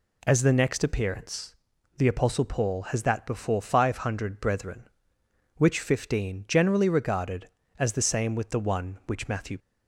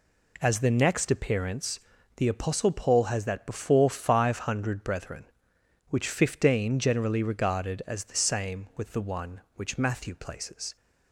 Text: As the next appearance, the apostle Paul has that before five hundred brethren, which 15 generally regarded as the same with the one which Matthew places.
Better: second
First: stops before "places"; at 9.5 s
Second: none

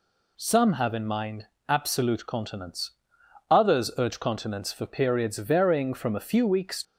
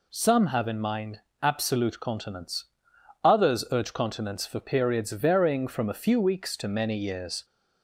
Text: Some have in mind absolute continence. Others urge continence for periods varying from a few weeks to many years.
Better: second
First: pauses between "mind" and "absolute"; slight; at 1.4 s; 0.24 s long // stops before "to many years"; at 6.8 s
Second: pauses between "mind" and "absolute"; slight; at 1.1 s; 0.24 s long

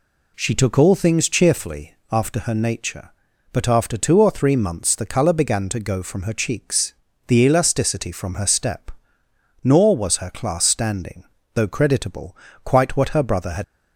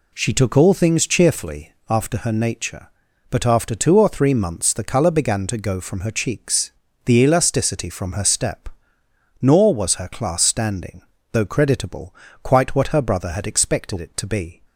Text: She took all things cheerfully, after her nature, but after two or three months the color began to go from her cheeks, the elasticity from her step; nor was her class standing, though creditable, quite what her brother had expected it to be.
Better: second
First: stops before "expected it to be"; at 13.6 s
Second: none

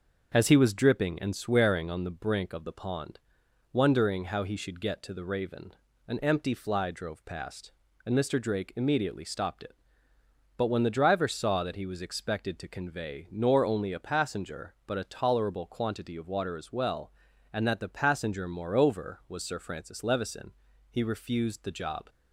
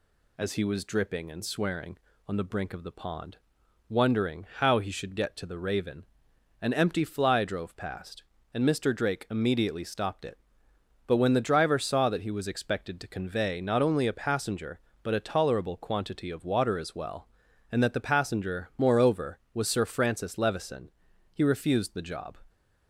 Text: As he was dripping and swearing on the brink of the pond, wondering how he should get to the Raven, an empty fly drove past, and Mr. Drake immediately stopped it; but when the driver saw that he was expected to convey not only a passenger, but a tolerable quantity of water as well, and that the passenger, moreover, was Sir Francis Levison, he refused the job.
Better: second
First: starts louder than the rest; until 1.3 s; 6.5 dB // says "nor" for "not"; at 13.3 s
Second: none

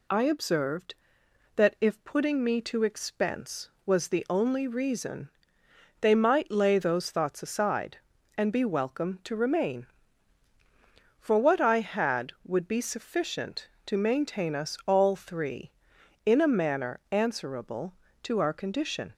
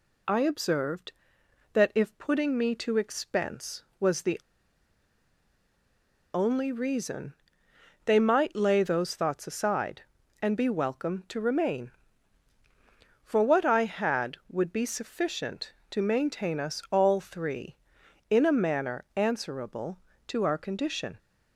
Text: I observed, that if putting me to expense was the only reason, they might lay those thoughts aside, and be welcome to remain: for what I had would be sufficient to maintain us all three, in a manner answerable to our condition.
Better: first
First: none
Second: pauses between "the" and "only"; strong; at 4.3 s; 1.9 s long

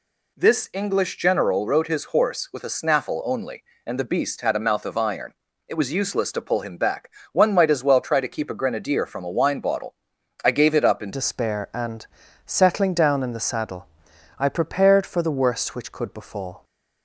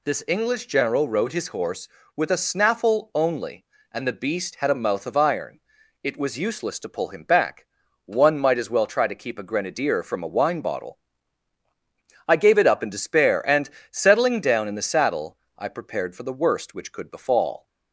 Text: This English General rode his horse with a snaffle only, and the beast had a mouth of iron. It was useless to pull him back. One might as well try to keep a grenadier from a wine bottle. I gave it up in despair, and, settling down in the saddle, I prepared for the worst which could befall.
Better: second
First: changes voice at "despair"; from 11.1 s on; 5.5 s long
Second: none

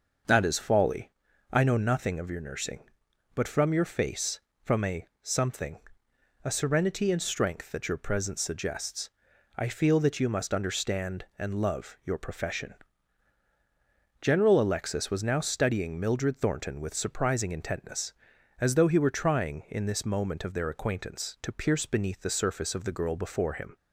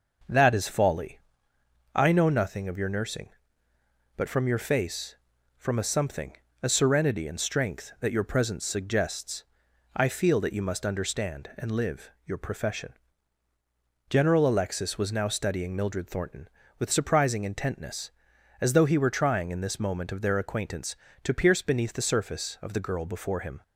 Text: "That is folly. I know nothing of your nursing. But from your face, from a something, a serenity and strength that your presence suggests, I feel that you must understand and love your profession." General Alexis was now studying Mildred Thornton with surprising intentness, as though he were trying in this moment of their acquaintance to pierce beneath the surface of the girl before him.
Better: first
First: starts louder than the rest; noticeable; until 1.6 s; 6 dB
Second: starts louder than the rest; until 2.0 s; 6.5 dB // says "live" for "love"; at 11.7 s

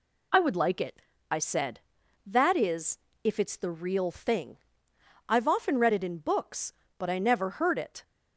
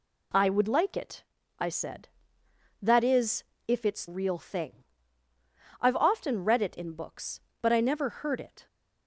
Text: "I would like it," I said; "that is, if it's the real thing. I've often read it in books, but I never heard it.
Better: first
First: none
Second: skips "the"; at 4.0 s

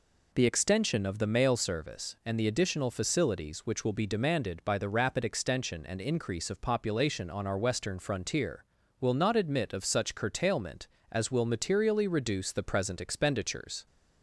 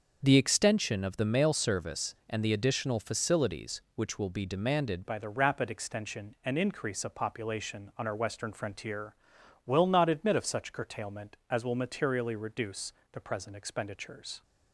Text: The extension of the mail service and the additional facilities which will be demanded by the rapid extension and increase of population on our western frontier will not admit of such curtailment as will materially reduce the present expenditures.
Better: first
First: none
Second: starts louder than the rest; until 1.2 s; 6.5 dB // changes voice at "by"; from 5.0 s on; 9.4 s long // pauses between "reduce" and "the"; slight; at 12.9 s; 0.20 s long

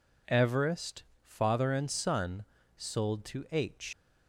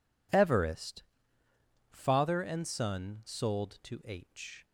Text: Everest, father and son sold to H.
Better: second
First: pauses between "son" and "sold"; slight; at 2.4 s; 0.32 s long // leaves "H" unfinished; at 3.9 s; 140 ms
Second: none

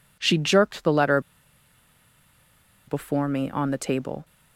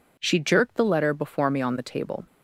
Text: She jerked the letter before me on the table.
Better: second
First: pauses between "letter" and "before"; strong; at 1.1 s; 1.6 s long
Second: none

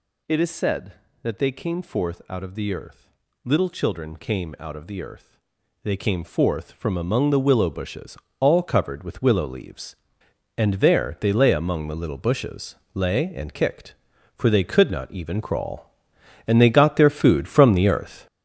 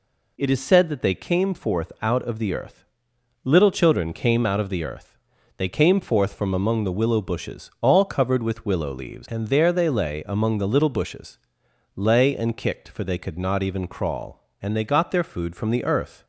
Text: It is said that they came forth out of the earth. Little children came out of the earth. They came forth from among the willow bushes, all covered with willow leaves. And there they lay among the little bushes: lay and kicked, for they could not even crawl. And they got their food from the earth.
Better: second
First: gets louder; throughout; 7 dB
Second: none

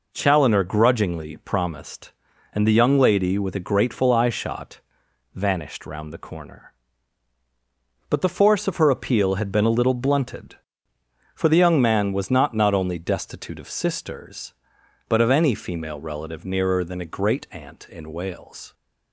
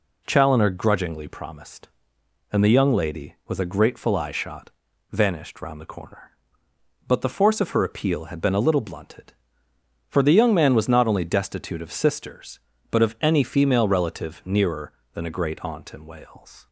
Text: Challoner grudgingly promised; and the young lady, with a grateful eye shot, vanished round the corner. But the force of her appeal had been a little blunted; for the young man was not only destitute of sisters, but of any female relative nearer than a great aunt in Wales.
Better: second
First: says "not" twice; at 12.5 s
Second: none

